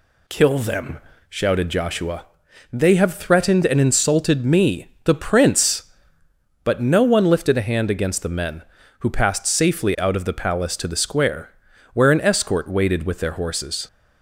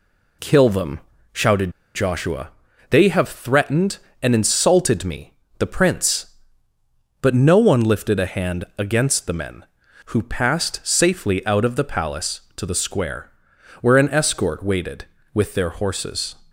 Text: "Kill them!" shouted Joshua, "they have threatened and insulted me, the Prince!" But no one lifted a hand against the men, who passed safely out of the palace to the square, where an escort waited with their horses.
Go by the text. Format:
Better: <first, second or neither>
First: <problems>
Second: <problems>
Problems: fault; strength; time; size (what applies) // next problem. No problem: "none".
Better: first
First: none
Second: pauses between "shouted" and "Joshua"; slight; at 1.6 s; 0.25 s long // pauses between "hand" and "against"; slight; at 8.6 s; 0.16 s long